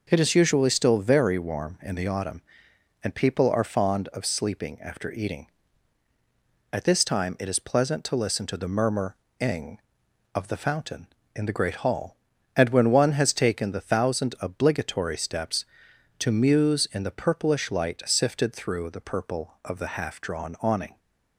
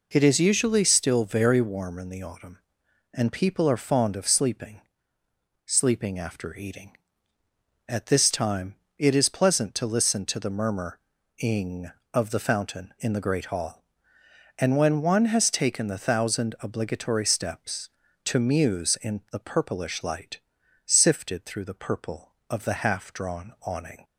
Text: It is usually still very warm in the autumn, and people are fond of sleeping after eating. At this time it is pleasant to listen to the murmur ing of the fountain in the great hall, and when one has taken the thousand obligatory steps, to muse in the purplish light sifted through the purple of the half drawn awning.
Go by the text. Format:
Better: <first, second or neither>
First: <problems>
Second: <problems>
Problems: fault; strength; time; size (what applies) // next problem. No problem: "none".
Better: first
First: pauses between "murmur" and "ing"; slight; at 9.1 s; 0.22 s long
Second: says "sleeping" twice; at 5.6 s // pauses between "time" and "it"; slight; at 8.7 s; 0.22 s long // pauses between "murmur" and "ing"; at 10.9 s; 0.38 s long // pauses between "light" and "sifted"; at 20.3 s; 0.44 s long